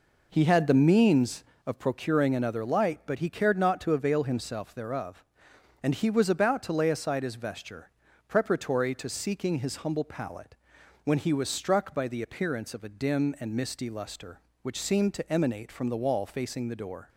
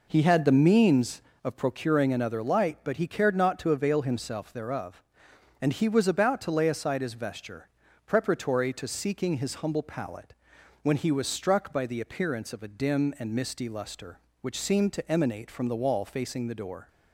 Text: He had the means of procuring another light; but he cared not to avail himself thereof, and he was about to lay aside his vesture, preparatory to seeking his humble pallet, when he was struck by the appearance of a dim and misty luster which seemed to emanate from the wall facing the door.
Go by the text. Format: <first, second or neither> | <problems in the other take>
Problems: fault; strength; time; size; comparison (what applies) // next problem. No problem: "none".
neither | none